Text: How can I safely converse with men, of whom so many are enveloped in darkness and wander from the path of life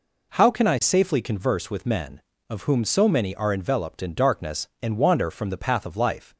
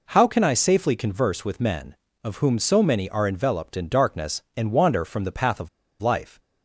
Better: first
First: none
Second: pauses between "of" and "life"; slight; at 5.6 s; 0.33 s long

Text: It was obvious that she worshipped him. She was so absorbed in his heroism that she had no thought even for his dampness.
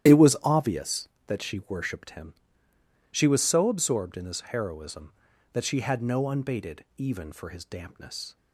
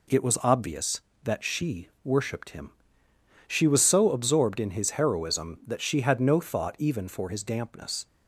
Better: second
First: starts louder than the rest; strong; until 1.3 s; 11.5 dB // says "unbated" for "thought"; at 6.2 s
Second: none

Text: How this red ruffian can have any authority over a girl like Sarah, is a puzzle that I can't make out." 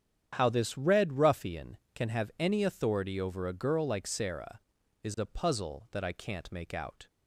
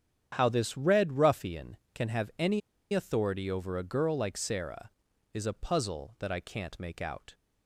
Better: first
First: starts louder than the rest; strong; until 1.4 s; 9 dB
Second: starts louder than the rest; strong; until 1.4 s; 9 dB // pauses between "any" and "authority"; slight; at 2.6 s; 0.33 s long

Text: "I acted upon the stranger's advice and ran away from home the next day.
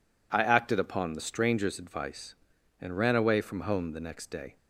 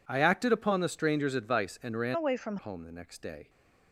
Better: first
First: none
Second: changes voice from "away" to "from"; from 2.1 to 2.5 s; 0.4 s long

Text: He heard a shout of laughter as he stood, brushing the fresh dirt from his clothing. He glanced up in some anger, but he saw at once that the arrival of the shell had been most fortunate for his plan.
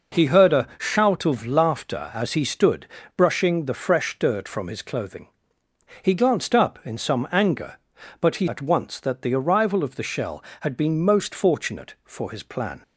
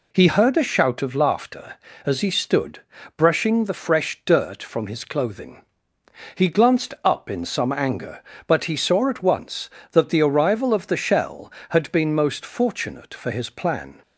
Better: second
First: skips "saw"; at 8.4 s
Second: none

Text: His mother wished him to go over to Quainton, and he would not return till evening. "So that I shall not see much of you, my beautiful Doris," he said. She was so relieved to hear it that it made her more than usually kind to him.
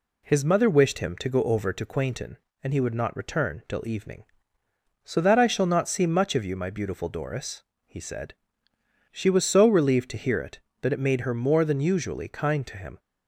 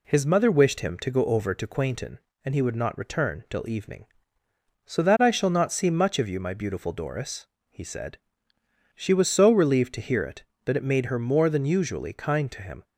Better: neither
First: none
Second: none

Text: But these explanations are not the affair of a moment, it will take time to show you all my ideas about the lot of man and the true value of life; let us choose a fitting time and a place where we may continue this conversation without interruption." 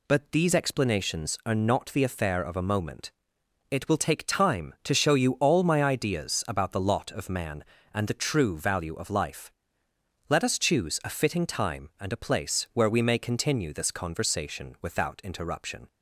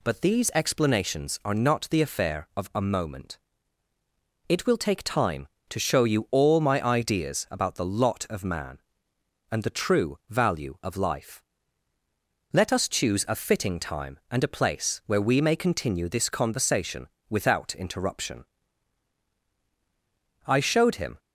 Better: first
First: none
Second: pauses between "conversation" and "without"; slight; at 17.0 s; 0.22 s long // goes on to say "I showed him"; noticeable; from 20.4 s on; 0.72 s long

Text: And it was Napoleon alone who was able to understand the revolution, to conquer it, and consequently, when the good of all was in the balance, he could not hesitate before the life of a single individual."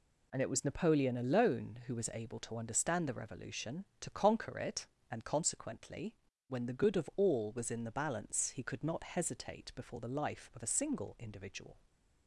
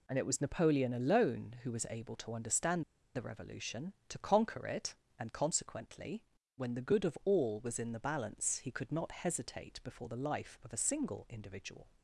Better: first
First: none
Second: pauses between "understand" and "the"; slight; at 2.8 s; 0.32 s long

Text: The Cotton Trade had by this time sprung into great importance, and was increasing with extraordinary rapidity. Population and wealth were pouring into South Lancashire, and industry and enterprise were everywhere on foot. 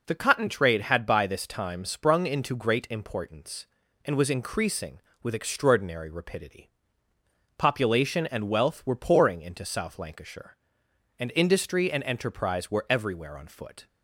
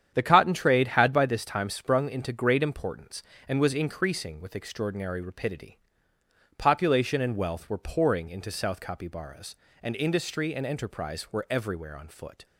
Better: first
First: none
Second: starts louder than the rest; strong; until 1.1 s; 9 dB // says "Capybaras" for "Lancashire"; at 8.7 s

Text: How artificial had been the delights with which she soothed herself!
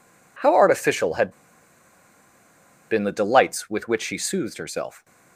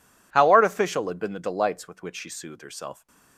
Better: second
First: pauses between "had" and "been"; strong; at 1.3 s; 1.5 s long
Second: none

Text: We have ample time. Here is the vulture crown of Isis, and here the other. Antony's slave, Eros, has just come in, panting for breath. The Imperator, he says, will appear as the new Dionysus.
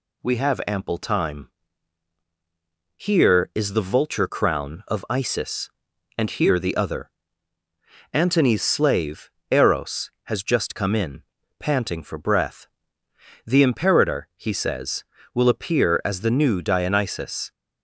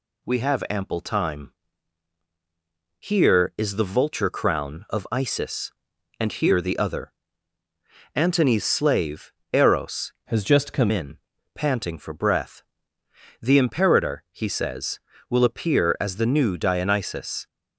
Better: first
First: none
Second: changes voice from "has" to "come"; from 10.2 to 10.9 s; 0.7 s long

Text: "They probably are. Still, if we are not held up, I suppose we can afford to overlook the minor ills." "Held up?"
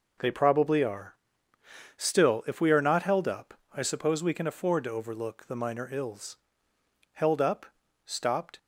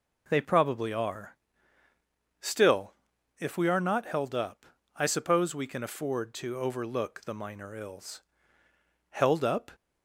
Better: second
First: goes on to say "Stopped"; from 8.0 s on; 0.54 s long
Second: none

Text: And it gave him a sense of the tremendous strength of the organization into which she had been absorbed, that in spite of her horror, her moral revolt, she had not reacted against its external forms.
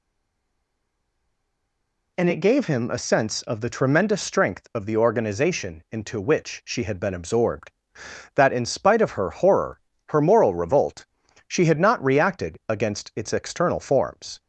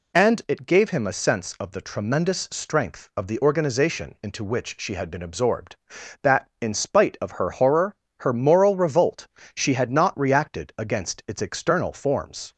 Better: second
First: stays silent before the first word; until 2.1 s; 2.1 s long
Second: none

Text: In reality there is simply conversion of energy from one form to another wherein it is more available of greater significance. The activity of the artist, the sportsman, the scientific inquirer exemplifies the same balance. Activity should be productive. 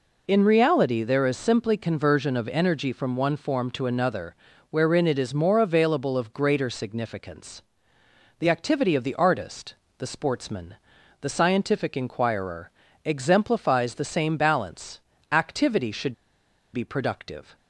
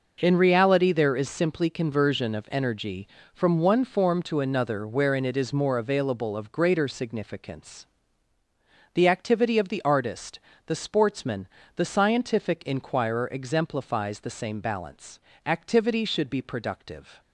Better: second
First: pauses between "another" and "wherein"; slight; at 4.3 s; 0.36 s long // pauses between "inquirer" and "exemplifies"; slight; at 12.7 s; 0.34 s long // pauses between "should" and "be"; noticeable; at 16.1 s; 0.59 s long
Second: none

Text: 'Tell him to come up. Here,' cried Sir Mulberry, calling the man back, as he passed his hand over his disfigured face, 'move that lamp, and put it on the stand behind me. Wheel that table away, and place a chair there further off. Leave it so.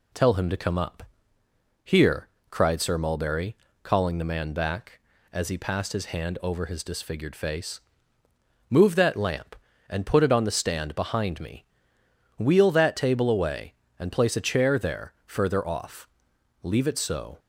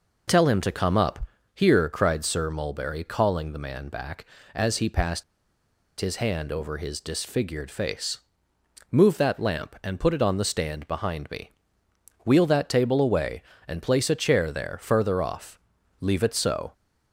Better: first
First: none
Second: pauses between "passed" and "his"; noticeable; at 5.2 s; 0.77 s long

